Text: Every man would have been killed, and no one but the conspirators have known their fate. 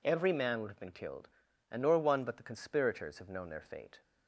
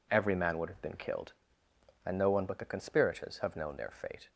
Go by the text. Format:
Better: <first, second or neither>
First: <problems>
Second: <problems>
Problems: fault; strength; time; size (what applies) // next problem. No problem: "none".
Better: second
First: says "nor" for "no"; at 1.8 s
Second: none